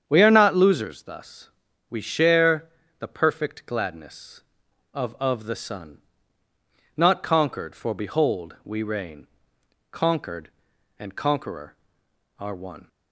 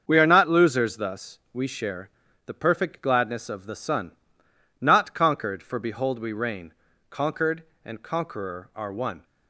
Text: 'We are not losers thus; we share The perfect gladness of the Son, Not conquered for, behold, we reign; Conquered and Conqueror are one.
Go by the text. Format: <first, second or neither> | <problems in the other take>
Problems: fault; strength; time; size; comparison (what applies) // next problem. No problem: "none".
second | starts louder than the rest; strong; until 1.0 s; 8 dB; also in the second // pauses between "share" and "The"; slight; at 2.6 s; 0.30 s long; slight in the second // says "of" twice; at 5.1 s